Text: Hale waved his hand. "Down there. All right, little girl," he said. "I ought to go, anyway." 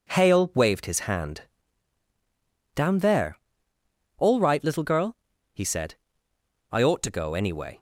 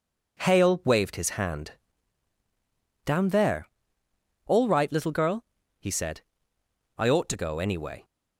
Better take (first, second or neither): neither